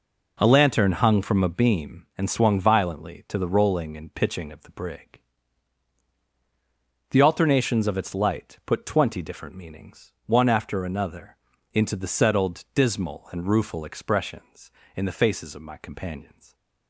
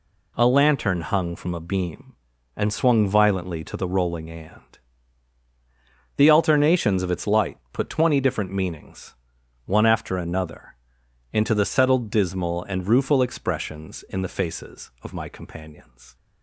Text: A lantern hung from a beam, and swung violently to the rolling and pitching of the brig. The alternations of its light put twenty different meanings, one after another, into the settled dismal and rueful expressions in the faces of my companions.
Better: first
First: none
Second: skips "pitching of the brig"; at 5.4 s

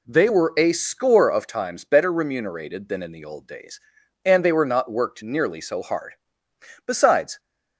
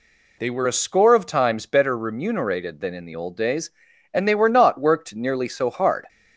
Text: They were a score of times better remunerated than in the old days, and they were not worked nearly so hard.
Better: second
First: goes on to say "Besides"; from 6.8 s on; 0.54 s long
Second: none

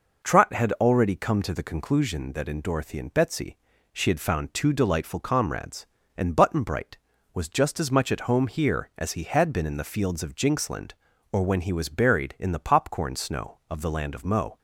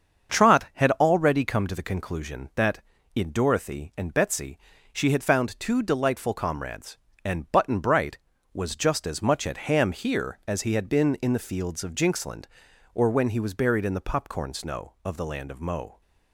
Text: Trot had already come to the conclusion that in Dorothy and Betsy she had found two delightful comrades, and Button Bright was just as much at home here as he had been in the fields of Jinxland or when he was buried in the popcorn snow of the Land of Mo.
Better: first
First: pauses between "Betsy" and "she"; slight; at 3.5 s; 0.36 s long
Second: starts louder than the rest; until 1.3 s; 7 dB // pauses between "Betsy" and "she"; slight; at 4.5 s; 0.36 s long // says "ham" for "home"; at 9.6 s

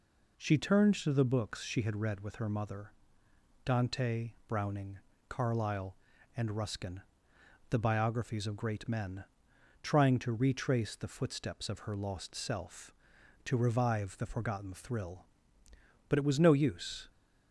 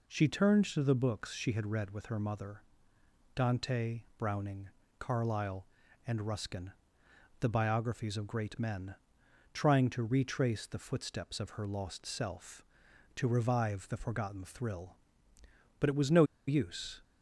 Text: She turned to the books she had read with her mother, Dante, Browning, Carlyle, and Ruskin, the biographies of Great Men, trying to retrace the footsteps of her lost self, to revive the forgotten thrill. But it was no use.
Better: first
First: none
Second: pauses between "no" and "use"; slight; at 16.2 s; 0.24 s long

